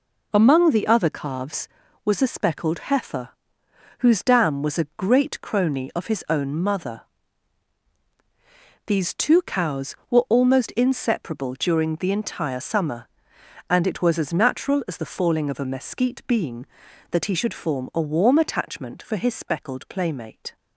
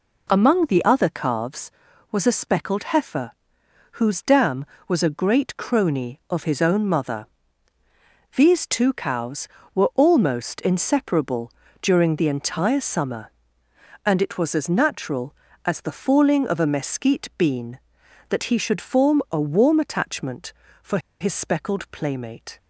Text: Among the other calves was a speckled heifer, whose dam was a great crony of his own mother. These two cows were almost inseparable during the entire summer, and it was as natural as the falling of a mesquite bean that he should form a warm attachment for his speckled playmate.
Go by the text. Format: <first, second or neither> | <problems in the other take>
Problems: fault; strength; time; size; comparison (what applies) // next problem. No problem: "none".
first | pauses between "inseparable" and "during"; slight; at 11.5 s; 0.30 s long // pauses between "for" and "his"; slight; at 20.9 s; 0.22 s long